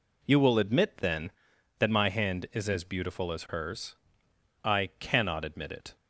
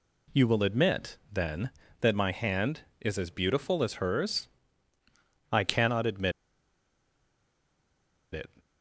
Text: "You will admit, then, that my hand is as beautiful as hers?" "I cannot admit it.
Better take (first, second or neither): first